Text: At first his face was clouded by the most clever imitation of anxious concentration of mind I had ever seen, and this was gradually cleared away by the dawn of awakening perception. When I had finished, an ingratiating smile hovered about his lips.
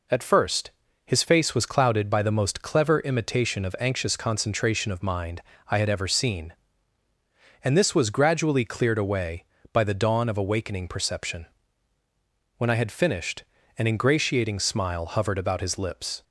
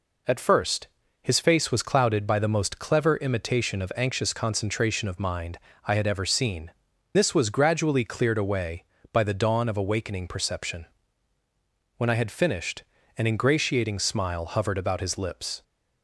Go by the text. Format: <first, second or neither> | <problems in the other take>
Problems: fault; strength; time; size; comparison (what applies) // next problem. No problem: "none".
first | pauses between "first" and "his"; slight; at 0.8 s; 0.34 s long; slight in the first // pauses between "mind" and "I"; slight; at 5.5 s; 0.30 s long; slight in the first // skips "and"; at 6.9 s